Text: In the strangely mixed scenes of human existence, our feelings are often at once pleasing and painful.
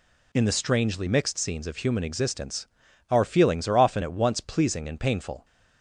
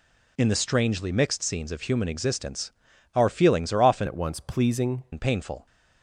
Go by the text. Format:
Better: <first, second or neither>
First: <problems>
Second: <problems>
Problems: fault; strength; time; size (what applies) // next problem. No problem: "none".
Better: first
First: none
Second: changes voice from "at" to "pleasing"; from 4.0 to 5.0 s; 1.0 s long